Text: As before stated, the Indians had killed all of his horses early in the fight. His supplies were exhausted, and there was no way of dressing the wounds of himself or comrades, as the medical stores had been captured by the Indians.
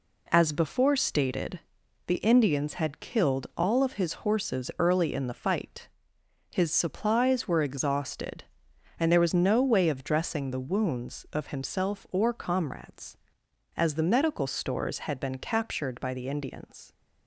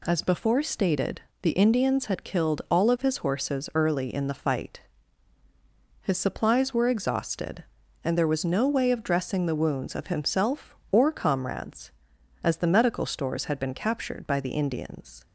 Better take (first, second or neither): neither